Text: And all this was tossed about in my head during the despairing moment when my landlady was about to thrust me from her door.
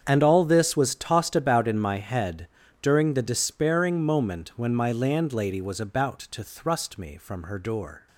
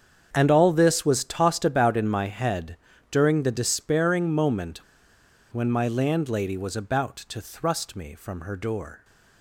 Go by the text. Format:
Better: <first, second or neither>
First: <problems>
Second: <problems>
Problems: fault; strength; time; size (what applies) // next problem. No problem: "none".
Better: first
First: starts louder than the rest; strong; until 1.0 s; 7.5 dB // pauses between "head" and "during"; slight; at 2.4 s; 0.32 s long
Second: starts louder than the rest; strong; until 1.3 s; 7.5 dB // pauses between "head" and "during"; slight; at 2.7 s; 0.32 s long // pauses between "moment" and "when"; noticeable; at 4.7 s; 0.72 s long